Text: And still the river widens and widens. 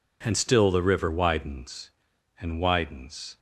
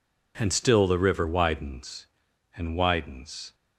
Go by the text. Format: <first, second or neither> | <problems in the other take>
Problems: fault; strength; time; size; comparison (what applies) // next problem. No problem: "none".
neither | none